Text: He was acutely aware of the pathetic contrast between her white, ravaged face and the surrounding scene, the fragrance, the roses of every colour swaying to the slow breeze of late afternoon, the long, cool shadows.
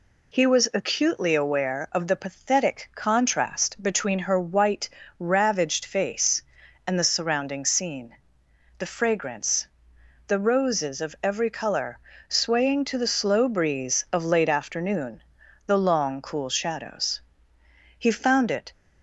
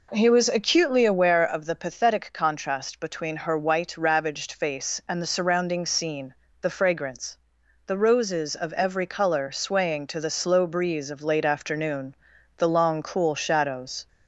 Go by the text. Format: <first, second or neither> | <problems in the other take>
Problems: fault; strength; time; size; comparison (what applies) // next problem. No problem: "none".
second | pauses between "colour" and "swaying"; slight; at 11.9 s; 0.30 s long // goes on to say "He found it"; noticeable; from 17.9 s on; 0.72 s long